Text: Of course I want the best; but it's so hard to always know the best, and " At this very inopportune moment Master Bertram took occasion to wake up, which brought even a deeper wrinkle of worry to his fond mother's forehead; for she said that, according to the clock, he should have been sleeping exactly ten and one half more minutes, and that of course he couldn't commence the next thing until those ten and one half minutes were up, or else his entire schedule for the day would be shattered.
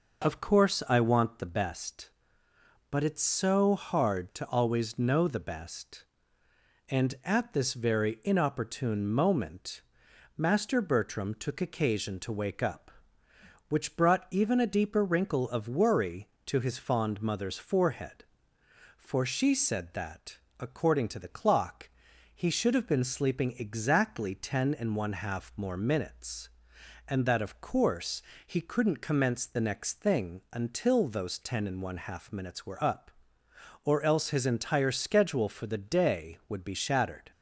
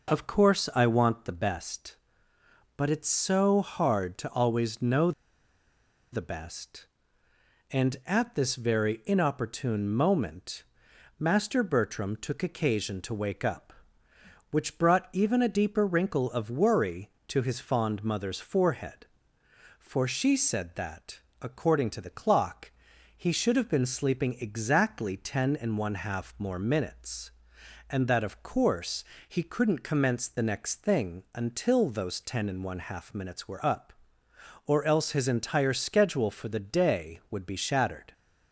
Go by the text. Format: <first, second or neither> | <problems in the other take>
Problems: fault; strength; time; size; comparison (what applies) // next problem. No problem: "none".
first | pauses between "know" and "the"; at 5.1 s; 1.0 s long // pauses between "moment" and "Master"; noticeable; at 10.6 s; 0.54 s long; noticeable in the first // pauses between "course" and "he"; slight; at 29.0 s; 0.28 s long; slight in the first